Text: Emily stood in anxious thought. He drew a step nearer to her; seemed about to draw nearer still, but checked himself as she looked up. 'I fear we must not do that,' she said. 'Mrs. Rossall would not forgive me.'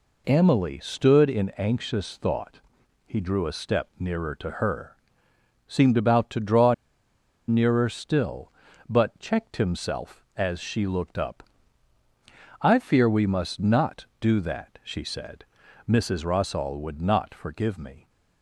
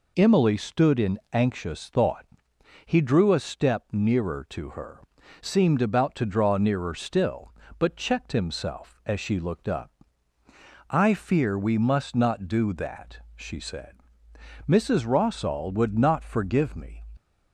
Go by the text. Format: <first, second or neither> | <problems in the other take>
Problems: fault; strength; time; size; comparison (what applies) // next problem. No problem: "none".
second | pauses between "draw" and "nearer"; noticeable; at 6.7 s; 0.74 s long